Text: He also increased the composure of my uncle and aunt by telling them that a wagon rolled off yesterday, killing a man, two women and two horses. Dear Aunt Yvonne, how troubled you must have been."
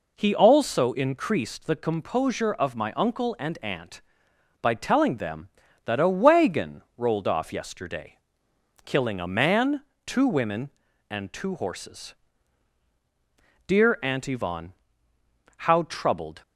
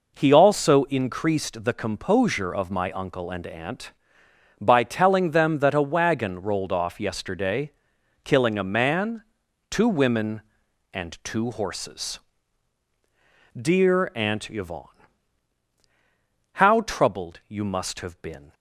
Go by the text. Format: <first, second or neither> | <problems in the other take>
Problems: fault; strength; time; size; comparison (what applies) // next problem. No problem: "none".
second | pauses between "wagon" and "rolled"; slight; at 6.8 s; 0.16 s long // stops before "you must have been"; at 16.4 s